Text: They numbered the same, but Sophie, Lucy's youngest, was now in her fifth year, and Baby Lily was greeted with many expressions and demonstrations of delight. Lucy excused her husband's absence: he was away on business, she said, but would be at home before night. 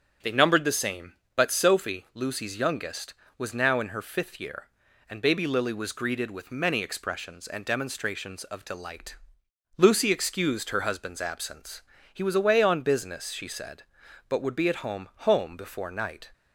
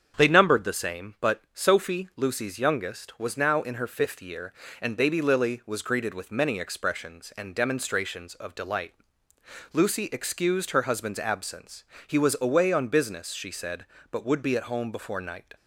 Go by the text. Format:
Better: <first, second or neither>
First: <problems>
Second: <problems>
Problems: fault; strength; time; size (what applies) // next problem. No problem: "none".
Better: second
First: starts louder than the rest; strong; until 1.4 s; 8 dB // says "home" twice; at 15.2 s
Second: starts louder than the rest; strong; until 1.2 s; 7.5 dB